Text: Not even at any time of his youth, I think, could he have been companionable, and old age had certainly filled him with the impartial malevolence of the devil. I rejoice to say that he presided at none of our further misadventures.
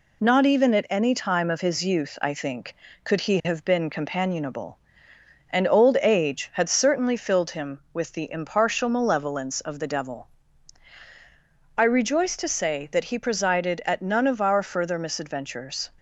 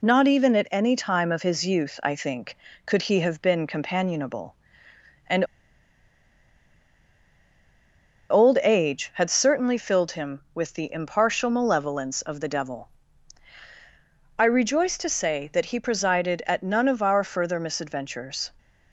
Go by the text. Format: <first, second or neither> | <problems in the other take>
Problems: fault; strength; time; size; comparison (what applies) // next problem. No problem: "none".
first | pauses between "and" and "old"; strong; at 5.4 s; 2.8 s long